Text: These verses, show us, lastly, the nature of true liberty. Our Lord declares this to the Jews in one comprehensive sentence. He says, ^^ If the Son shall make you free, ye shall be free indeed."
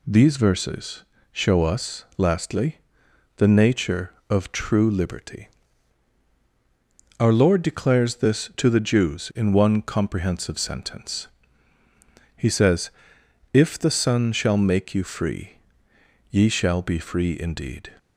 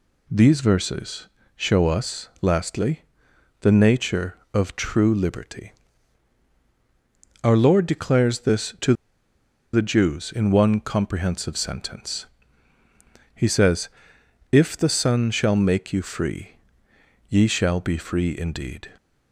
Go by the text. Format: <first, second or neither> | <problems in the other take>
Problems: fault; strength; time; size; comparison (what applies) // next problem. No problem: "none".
first | pauses between "to" and "the"; noticeable; at 8.9 s; 0.80 s long